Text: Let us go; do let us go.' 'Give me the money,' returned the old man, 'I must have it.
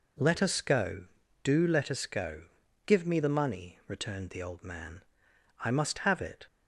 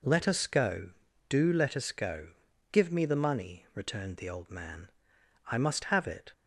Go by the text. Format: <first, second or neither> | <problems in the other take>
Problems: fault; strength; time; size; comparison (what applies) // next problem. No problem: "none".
neither | none